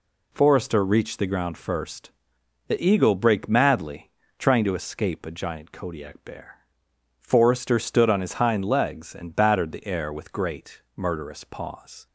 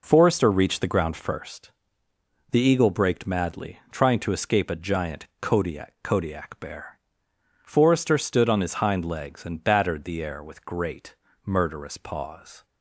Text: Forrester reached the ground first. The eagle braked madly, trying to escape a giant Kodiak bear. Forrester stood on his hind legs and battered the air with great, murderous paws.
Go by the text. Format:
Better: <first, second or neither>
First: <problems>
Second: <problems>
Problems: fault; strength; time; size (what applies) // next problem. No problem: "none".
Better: first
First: none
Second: says "Kodiak" twice; at 6.0 s